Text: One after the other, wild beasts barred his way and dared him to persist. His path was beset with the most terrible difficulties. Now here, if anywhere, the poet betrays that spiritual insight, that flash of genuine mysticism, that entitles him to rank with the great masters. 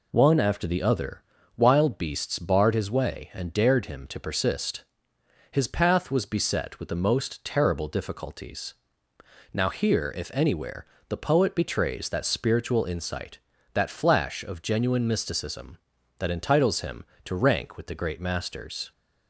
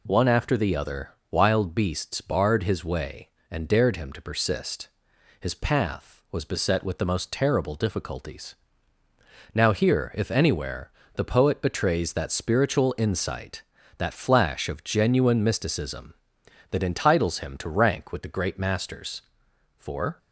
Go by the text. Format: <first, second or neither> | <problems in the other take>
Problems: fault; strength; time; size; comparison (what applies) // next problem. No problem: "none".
first | goes on to say "For"; slight; from 19.7 s on; 0.42 s long